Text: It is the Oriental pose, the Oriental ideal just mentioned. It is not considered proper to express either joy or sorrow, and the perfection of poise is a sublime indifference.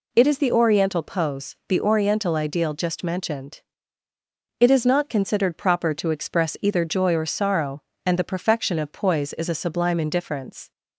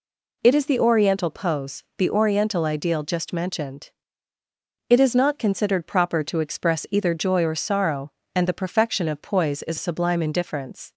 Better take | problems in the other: first | skips "a"; at 9.7 s

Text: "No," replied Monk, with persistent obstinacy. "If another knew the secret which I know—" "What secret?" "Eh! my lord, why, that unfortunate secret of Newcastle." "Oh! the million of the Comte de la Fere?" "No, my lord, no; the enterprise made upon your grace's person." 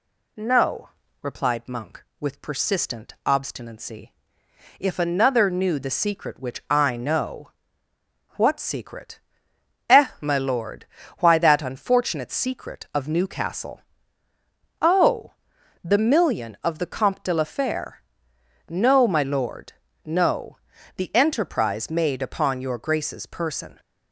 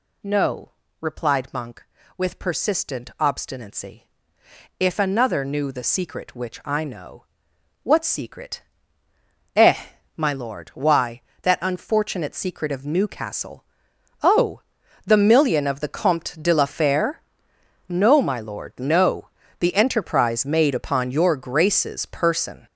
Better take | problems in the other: first | gets louder; strong; throughout; 8 dB

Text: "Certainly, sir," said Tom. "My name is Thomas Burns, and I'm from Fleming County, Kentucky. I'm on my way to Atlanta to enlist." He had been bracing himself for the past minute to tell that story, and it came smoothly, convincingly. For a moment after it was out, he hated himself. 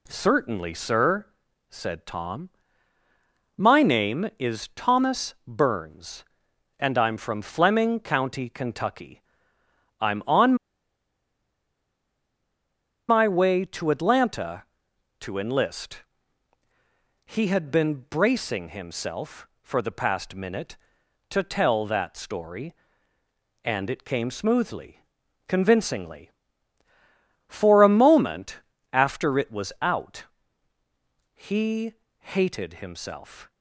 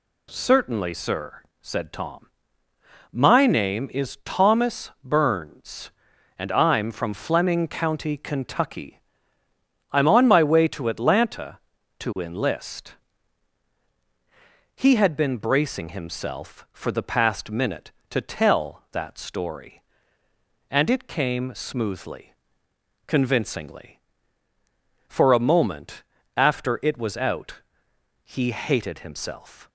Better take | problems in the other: second | pauses between "on" and "my"; strong; at 10.5 s; 2.5 s long // pauses between "moment" and "after"; slight; at 28.6 s; 0.30 s long; slight in the second // pauses between "he" and "hated"; slight; at 31.9 s; 0.26 s long

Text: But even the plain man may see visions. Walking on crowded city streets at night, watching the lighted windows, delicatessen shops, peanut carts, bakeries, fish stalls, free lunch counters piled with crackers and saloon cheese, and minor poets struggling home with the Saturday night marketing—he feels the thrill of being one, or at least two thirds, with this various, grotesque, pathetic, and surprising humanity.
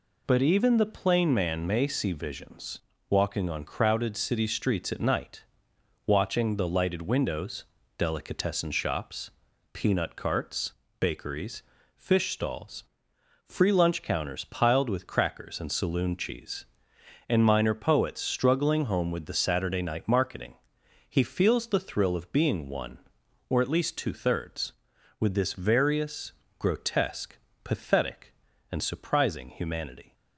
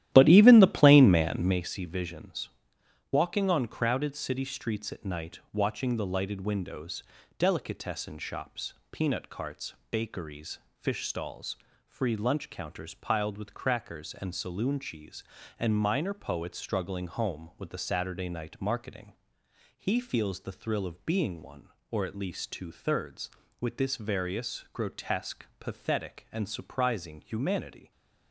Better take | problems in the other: first | starts louder than the rest; strong; until 1.6 s; 13 dB

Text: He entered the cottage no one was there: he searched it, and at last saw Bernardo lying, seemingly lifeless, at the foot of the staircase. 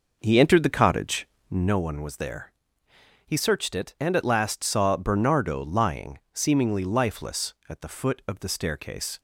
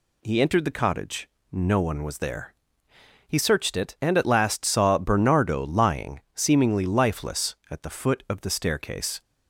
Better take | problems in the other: second | starts louder than the rest; noticeable; until 1.8 s; 5.5 dB // pauses between "cottage" and "no"; slight; at 1.2 s; 0.22 s long; slight in the second

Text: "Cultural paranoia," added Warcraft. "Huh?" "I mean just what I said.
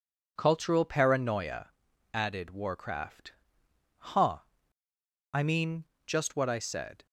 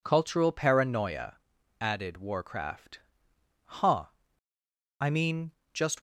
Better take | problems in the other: first | pauses between "mean" and "just"; slight; at 5.5 s; 0.20 s long; slight in the first // stops before "what I said"; at 5.9 s

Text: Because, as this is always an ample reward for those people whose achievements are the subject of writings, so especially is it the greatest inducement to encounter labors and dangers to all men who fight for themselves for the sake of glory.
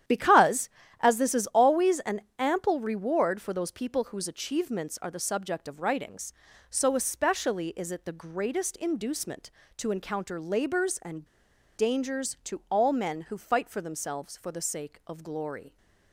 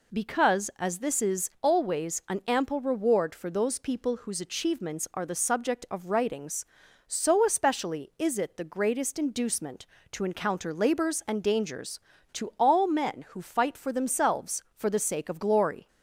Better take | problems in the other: second | starts louder than the rest; strong; until 1.3 s; 10.5 dB // pauses between "an" and "ample"; slight; at 2.2 s; 0.18 s long // pauses between "and" and "dangers"; noticeable; at 11.2 s; 0.50 s long

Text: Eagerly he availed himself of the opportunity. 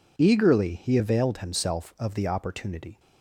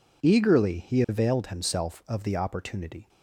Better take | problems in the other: neither | none

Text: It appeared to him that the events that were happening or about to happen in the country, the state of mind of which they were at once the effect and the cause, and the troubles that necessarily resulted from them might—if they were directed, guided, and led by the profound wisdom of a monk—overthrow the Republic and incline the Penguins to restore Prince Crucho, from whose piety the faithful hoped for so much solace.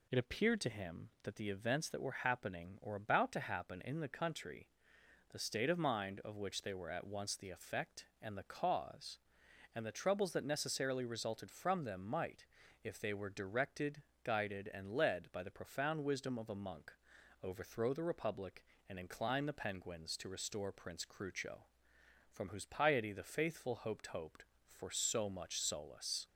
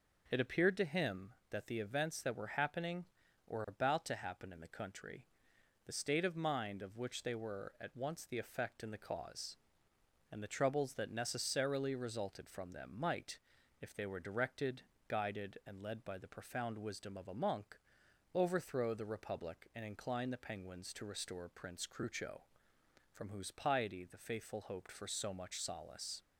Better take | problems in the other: second | says "hoped" twice; at 24.0 s

